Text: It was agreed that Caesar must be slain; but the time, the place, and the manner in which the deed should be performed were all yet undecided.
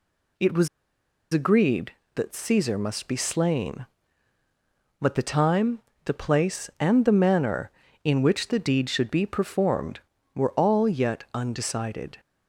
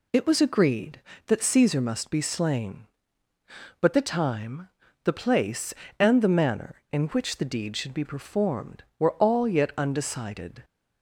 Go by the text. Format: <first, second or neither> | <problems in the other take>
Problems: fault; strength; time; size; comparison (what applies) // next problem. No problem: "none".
second | pauses between "was" and "agreed"; noticeable; at 0.6 s; 0.64 s long